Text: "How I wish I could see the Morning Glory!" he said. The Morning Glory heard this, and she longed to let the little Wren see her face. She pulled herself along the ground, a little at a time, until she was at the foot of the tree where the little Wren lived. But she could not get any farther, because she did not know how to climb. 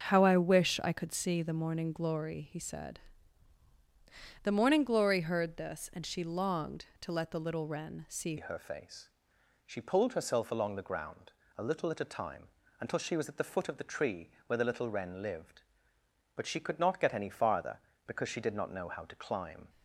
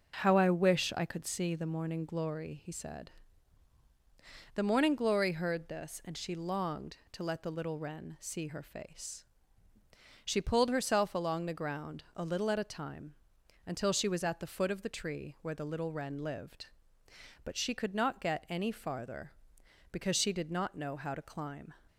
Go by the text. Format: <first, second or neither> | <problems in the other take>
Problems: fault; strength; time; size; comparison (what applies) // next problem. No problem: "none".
second | starts louder than the rest; until 1.1 s; 6 dB // changes voice at "her"; from 8.3 s on; 11.3 s long // pauses between "tree" and "where"; slight; at 14.2 s; 0.18 s long